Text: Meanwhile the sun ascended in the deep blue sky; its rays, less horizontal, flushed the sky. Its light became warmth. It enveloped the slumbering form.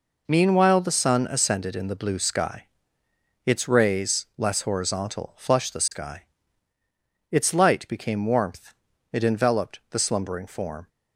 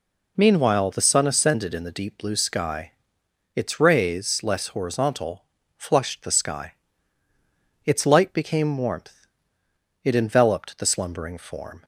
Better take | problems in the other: second | skips "deep"; at 1.9 s

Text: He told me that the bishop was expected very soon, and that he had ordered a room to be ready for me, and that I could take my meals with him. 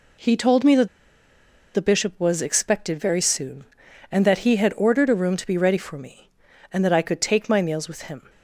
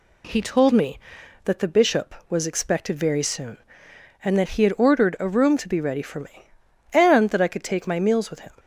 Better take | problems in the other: second | pauses between "that" and "the"; noticeable; at 0.8 s; 0.86 s long

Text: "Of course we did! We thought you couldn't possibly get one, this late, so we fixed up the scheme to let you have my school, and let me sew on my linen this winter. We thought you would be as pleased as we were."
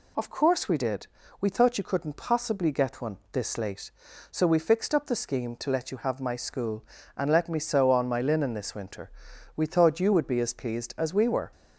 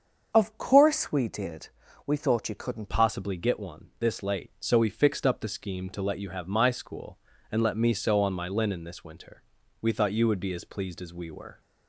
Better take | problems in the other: first | starts louder than the rest; until 1.3 s; 7 dB // changes voice at "possibly"; from 2.8 s on; 8.8 s long

